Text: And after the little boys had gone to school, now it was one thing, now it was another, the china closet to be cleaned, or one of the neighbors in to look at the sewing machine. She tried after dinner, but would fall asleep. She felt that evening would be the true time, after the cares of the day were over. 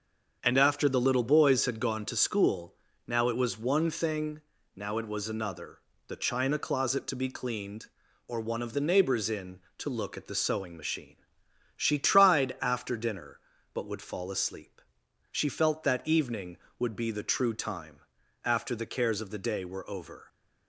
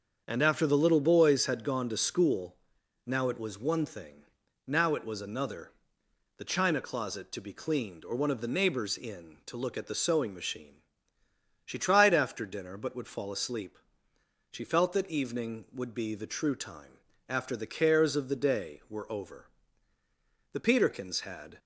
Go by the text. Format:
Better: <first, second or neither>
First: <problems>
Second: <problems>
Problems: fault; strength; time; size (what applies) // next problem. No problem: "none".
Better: first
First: starts louder than the rest; until 1.4 s; 7 dB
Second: starts louder than the rest; strong; until 1.2 s; 7 dB // goes on to say "The Peterkins had"; noticeable; from 20.5 s on; 1.0 s long